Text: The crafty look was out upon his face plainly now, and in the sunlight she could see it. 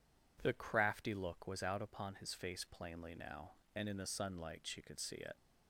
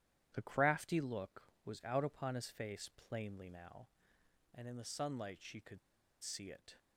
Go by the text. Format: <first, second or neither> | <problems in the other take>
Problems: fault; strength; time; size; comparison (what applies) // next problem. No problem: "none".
first | pauses between "could" and "see"; at 5.7 s; 0.44 s long